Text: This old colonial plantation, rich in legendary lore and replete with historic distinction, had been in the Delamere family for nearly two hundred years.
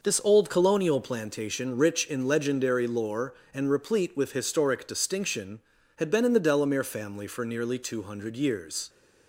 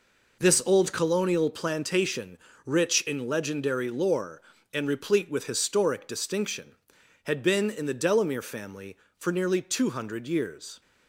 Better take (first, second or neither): neither